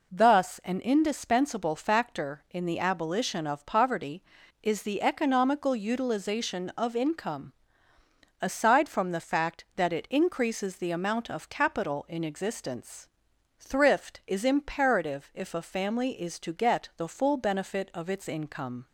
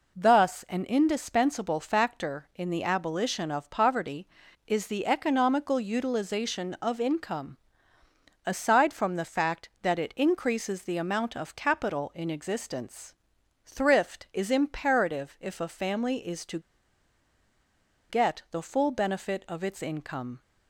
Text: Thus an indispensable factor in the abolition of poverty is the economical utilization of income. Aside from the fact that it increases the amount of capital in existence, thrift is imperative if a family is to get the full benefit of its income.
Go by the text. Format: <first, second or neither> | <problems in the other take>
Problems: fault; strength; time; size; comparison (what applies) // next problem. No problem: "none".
first | pauses between "to" and "get"; strong; at 16.5 s; 1.4 s long